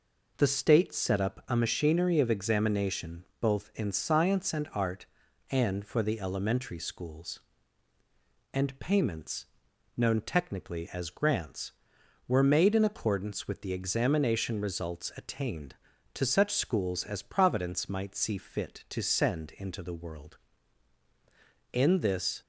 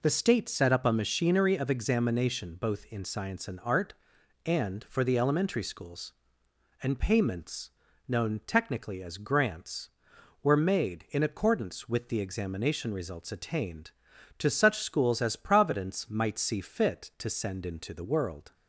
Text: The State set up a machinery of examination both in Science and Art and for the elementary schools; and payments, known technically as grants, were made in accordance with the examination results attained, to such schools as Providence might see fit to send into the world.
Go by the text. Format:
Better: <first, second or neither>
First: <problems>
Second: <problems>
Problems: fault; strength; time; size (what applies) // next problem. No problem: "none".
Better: second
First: pauses between "examination" and "both"; slight; at 3.2 s; 0.16 s long // goes on to say "In this"; noticeable; from 21.7 s on; 0.68 s long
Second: none